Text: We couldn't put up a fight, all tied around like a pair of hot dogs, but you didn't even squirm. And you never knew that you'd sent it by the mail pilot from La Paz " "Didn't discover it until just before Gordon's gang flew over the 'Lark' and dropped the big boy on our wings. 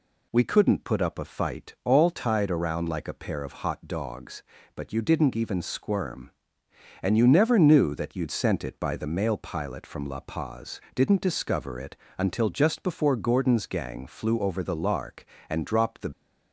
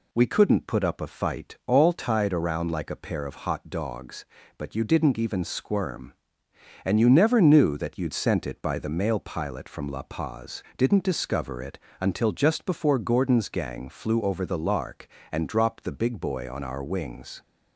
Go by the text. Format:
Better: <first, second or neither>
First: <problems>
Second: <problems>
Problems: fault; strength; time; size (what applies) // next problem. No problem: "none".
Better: second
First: pauses between "it" and "until"; slight; at 11.9 s; 0.22 s long // stops before "big boy on our wings"; at 16.1 s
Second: pauses between "it" and "until"; slight; at 11.7 s; 0.22 s long